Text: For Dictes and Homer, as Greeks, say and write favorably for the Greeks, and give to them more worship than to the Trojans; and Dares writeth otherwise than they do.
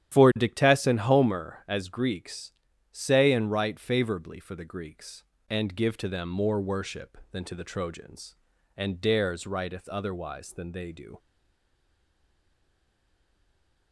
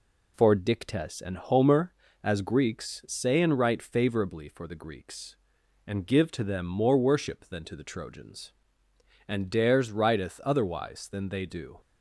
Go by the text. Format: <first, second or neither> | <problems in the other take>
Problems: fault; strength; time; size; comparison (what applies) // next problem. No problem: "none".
second | starts louder than the rest; strong; until 1.1 s; 11 dB // stays silent after the last word; strong; from 11.1 s on; 2.8 s long